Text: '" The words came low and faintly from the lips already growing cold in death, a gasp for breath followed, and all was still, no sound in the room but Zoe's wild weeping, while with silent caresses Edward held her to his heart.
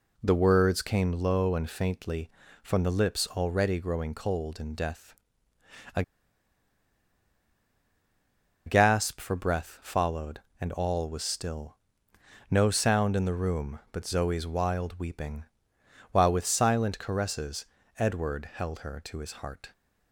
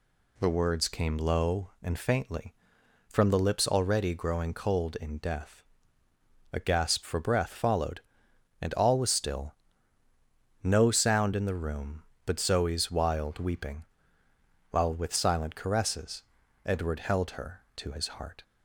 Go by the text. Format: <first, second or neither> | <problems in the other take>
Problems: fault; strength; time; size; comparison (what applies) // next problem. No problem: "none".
second | pauses between "a" and "gasp"; strong; at 6.0 s; 2.6 s long // pauses between "caresses" and "Edward"; slight; at 17.6 s; 0.32 s long; also in the second